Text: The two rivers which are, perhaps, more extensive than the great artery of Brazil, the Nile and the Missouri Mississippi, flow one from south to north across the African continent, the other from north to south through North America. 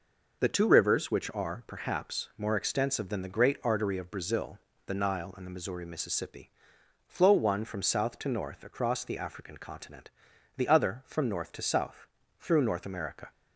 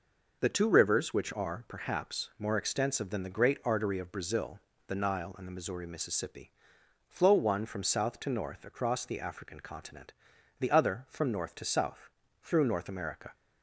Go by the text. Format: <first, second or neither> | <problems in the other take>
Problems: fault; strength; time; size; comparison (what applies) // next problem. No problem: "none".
neither | pauses between "south" and "through"; slight; the same in both